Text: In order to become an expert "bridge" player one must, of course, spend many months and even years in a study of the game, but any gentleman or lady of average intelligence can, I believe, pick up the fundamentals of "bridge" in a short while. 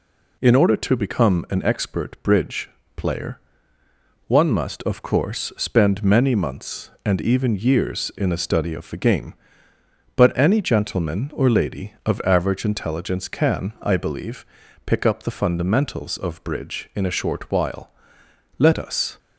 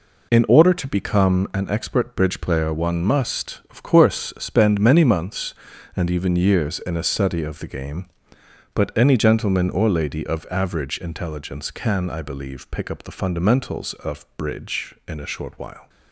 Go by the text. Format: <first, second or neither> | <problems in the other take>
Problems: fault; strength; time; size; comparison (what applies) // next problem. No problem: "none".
second | pauses between "bridge" and "player"; slight; at 2.7 s; 0.24 s long // pauses between "player" and "one"; noticeable; at 3.4 s; 0.88 s long // goes on to say "Let us"; from 18.5 s on; 0.60 s long